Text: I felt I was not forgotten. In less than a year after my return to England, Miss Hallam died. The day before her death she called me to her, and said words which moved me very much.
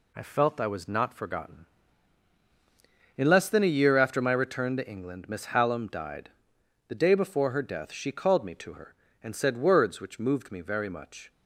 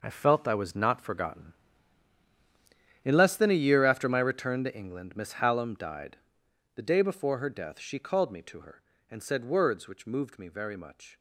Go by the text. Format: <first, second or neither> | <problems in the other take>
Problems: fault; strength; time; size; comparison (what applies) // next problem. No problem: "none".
first | gets quieter; strong; throughout; 11.5 dB